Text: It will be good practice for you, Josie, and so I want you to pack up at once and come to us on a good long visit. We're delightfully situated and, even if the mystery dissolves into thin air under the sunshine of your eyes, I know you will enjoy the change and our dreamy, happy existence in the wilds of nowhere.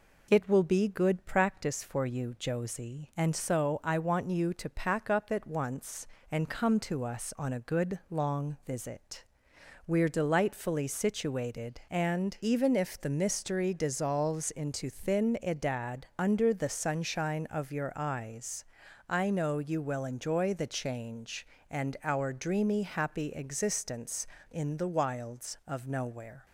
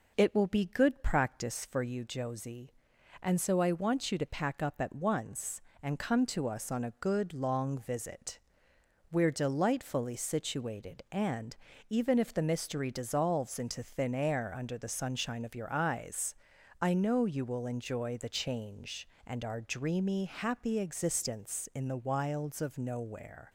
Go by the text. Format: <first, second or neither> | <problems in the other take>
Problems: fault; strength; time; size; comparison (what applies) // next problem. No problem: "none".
second | says "edad" for "air"; at 15.4 s